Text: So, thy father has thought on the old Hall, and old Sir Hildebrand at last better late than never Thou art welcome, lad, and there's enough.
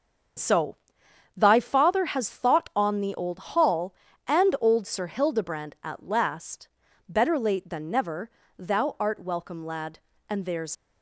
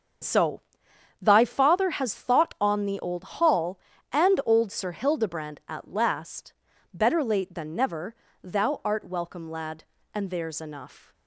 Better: second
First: starts louder than the rest; until 1.9 s; 7 dB // pauses between "last" and "better"; at 6.6 s; 0.40 s long // pauses between "never" and "Thou"; slight; at 8.2 s; 0.30 s long // stops before "enough"; at 10.7 s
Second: starts louder than the rest; strong; until 1.8 s; 7 dB // pauses between "last" and "better"; at 6.5 s; 0.40 s long // pauses between "never" and "Thou"; slight; at 8.1 s; 0.30 s long

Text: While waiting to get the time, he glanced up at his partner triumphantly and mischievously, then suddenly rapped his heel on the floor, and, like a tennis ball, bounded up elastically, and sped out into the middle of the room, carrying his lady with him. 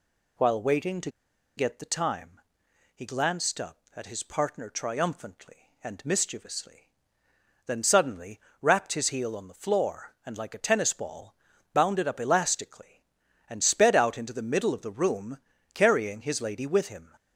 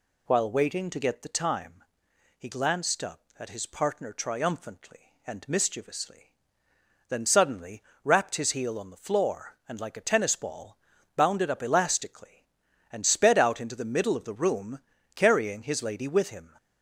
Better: second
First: pauses between "to" and "get"; noticeable; at 1.0 s; 0.47 s long // pauses between "suddenly" and "rapped"; slight; at 8.3 s; 0.22 s long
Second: pauses between "suddenly" and "rapped"; slight; at 7.8 s; 0.22 s long

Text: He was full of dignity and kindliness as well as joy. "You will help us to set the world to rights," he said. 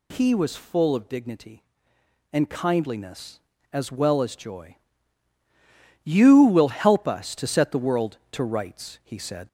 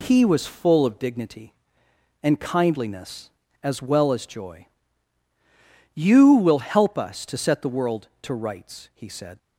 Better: second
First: gets louder; slight; throughout; 2.5 dB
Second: none

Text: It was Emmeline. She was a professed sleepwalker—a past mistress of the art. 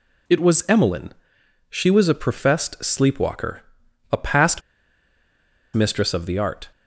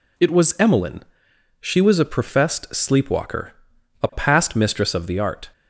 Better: second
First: pauses between "past" and "mistress"; at 4.6 s; 1.1 s long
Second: none

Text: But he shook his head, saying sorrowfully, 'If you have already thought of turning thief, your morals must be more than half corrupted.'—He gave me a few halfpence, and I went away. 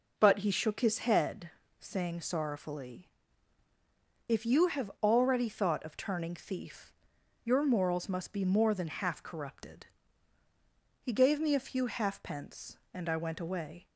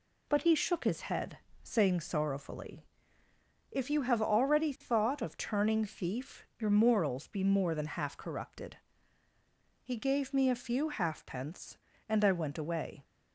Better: first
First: none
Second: skips "must"; at 7.2 s

